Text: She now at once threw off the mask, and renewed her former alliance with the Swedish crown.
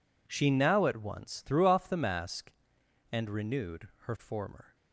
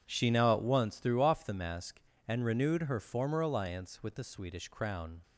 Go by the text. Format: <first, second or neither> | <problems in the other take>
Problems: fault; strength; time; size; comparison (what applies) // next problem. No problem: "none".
second | stops before "alliance with the Swedish crown"; at 4.7 s